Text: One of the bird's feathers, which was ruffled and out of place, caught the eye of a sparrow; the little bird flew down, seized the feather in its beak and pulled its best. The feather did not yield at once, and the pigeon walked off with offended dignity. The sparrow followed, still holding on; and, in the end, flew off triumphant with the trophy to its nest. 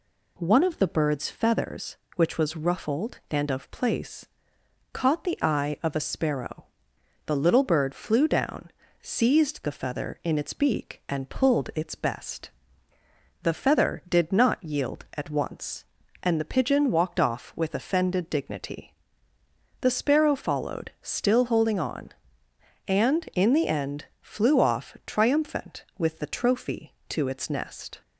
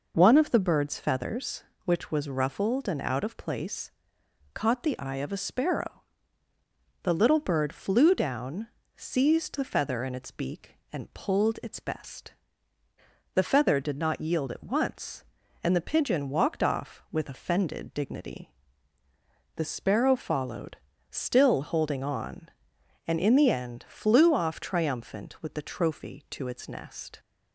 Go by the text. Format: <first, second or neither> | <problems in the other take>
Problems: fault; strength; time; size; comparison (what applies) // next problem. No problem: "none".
second | skips "out"; at 3.5 s